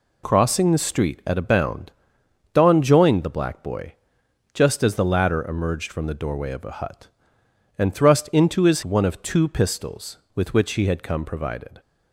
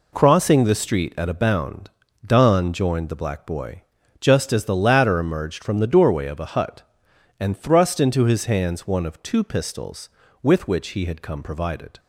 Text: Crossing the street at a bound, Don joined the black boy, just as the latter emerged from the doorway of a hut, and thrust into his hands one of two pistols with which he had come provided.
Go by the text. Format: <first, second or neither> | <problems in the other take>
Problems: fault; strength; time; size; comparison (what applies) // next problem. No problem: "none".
second | skips "hands"; at 8.8 s